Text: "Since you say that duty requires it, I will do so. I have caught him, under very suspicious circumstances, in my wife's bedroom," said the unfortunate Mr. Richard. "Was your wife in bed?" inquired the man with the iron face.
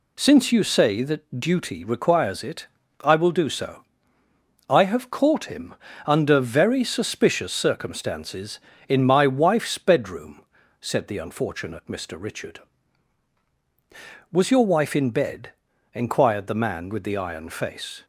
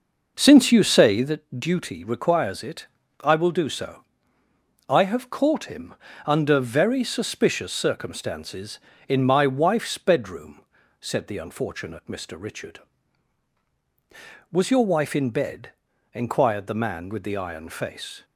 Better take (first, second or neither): first